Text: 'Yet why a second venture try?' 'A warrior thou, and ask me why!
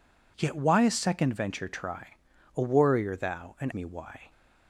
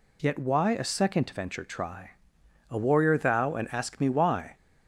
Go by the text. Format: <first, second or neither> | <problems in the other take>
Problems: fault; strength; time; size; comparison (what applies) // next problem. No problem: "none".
second | skips "ask"; at 3.7 s